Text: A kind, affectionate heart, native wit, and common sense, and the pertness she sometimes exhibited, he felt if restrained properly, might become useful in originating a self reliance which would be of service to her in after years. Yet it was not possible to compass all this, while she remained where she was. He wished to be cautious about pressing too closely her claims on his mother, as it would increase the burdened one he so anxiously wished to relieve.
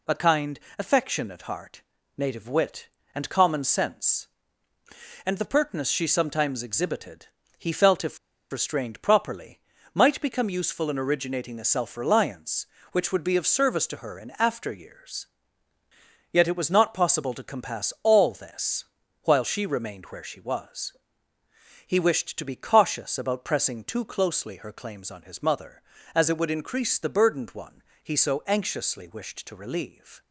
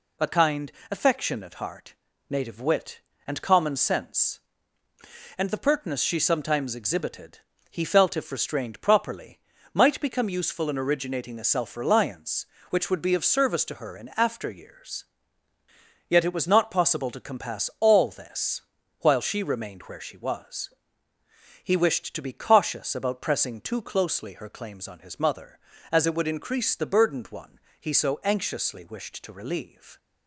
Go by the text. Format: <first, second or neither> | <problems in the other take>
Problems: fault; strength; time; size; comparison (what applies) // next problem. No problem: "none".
second | pauses between "if" and "restrained"; slight; at 8.1 s; 0.34 s long // pauses between "one" and "he"; slight; at 27.8 s; 0.22 s long; slight in the second